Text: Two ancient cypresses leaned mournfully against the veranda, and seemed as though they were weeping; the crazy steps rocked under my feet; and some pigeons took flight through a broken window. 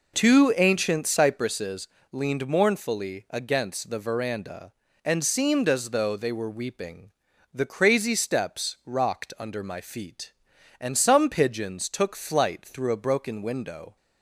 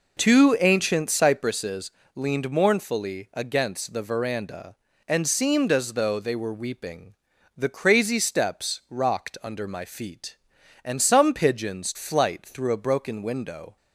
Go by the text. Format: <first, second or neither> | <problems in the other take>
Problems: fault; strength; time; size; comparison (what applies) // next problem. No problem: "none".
first | pauses between "cypresses" and "leaned"; slight; at 1.9 s; 0.24 s long; slight in the first // skips "took"; at 11.9 s